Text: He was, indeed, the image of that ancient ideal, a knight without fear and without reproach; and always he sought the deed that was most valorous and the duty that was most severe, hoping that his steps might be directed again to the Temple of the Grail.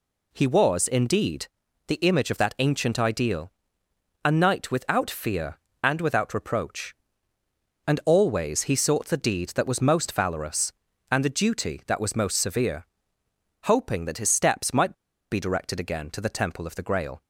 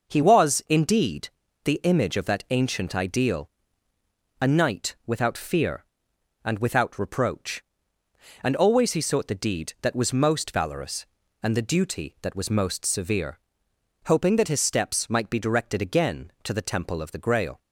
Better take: second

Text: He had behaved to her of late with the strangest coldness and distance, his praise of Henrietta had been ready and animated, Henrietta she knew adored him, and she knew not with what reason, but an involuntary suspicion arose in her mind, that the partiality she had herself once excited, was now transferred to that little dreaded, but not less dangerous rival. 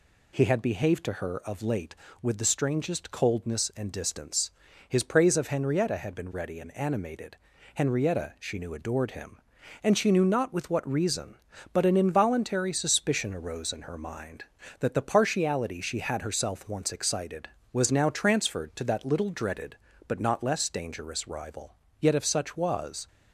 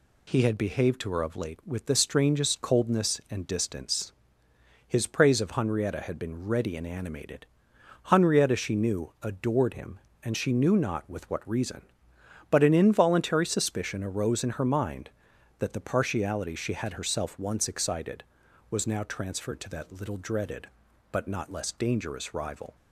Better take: second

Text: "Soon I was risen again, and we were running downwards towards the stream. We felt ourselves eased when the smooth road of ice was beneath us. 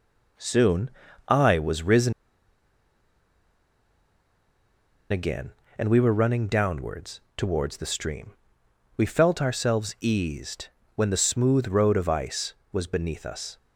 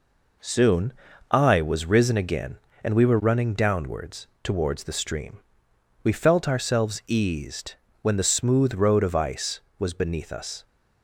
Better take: second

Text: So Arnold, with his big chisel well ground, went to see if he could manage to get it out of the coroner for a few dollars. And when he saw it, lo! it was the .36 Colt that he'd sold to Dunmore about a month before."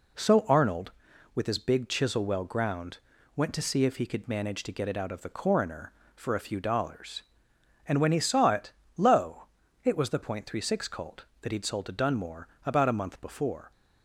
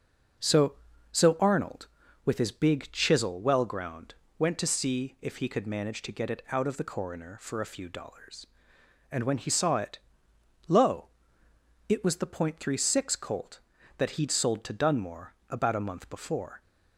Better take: first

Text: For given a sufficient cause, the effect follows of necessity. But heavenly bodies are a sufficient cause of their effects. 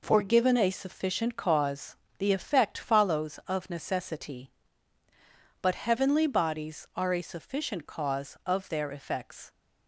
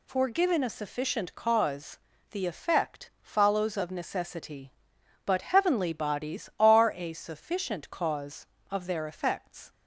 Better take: neither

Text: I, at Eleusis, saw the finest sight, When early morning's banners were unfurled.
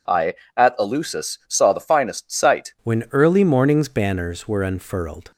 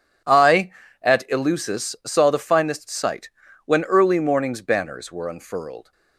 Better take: second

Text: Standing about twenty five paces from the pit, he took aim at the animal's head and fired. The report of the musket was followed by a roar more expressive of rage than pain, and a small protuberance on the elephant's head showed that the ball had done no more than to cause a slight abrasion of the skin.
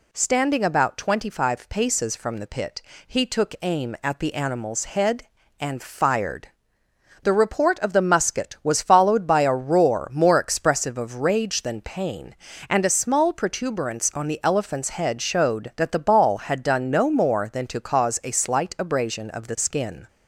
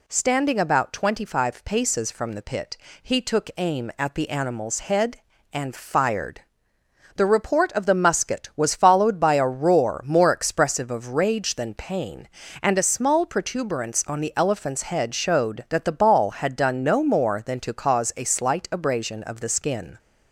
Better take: neither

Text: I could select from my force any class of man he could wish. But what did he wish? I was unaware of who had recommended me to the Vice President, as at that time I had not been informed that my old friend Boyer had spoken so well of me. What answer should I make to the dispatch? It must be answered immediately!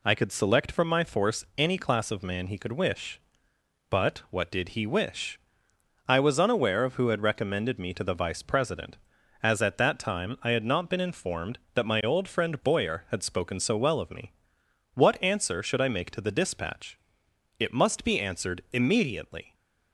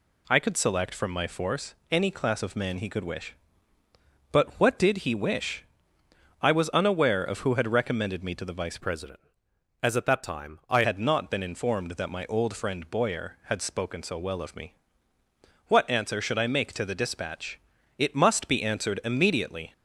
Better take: first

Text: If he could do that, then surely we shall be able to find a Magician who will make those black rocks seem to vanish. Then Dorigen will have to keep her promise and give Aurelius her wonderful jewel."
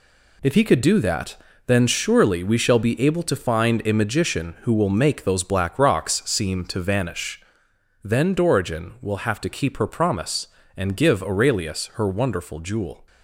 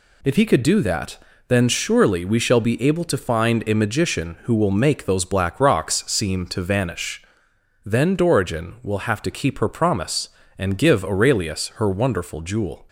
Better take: second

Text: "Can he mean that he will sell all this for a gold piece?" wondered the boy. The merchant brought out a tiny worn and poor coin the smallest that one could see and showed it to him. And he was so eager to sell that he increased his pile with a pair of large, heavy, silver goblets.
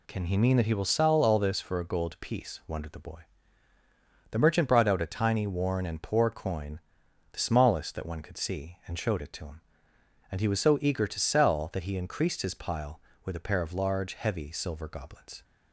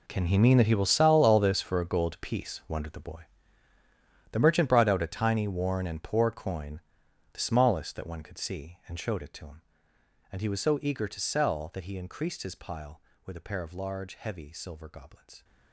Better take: first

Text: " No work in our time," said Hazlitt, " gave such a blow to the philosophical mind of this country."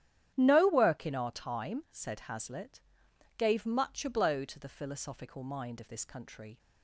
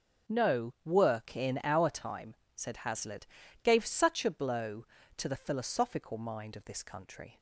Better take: second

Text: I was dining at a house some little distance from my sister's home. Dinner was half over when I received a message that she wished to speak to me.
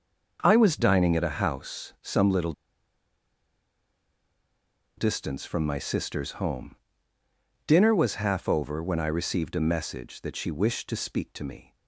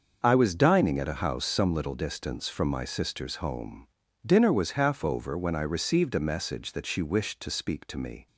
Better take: second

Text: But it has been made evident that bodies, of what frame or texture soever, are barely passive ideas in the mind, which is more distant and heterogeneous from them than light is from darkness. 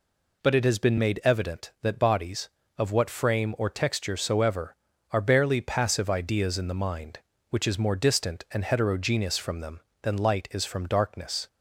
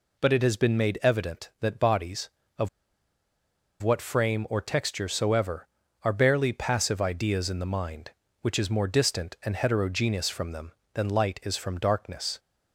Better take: first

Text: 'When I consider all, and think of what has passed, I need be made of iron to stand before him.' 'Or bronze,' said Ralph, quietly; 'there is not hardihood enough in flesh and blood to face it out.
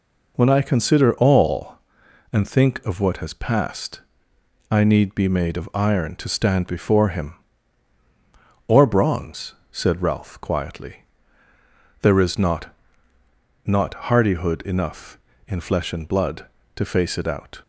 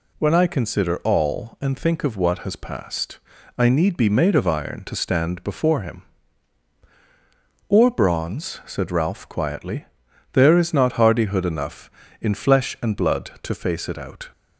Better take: second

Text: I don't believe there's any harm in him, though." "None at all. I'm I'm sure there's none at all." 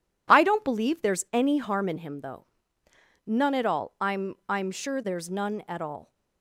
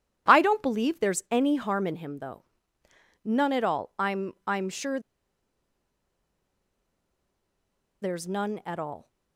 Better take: first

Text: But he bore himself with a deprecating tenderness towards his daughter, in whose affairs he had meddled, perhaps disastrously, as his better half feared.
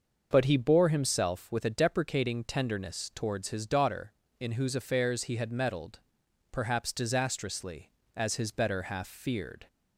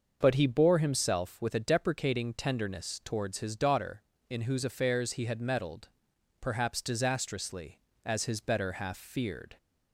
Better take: neither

